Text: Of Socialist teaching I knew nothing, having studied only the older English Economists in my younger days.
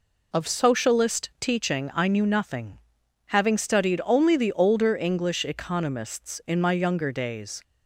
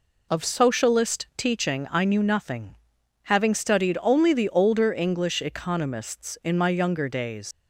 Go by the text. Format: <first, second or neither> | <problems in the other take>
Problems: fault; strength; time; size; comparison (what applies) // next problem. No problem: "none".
first | leaves "days" unfinished; at 7.5 s; 85 ms